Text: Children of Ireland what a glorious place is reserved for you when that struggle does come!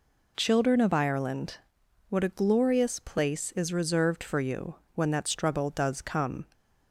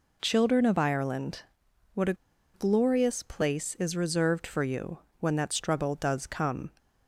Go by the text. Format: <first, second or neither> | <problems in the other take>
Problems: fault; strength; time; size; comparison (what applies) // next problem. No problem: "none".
first | pauses between "Ireland" and "what"; noticeable; at 1.4 s; 0.50 s long; noticeable in the first // pauses between "a" and "glorious"; at 2.1 s; 0.40 s long // pauses between "you" and "when"; slight; at 4.9 s; 0.22 s long; slight in the first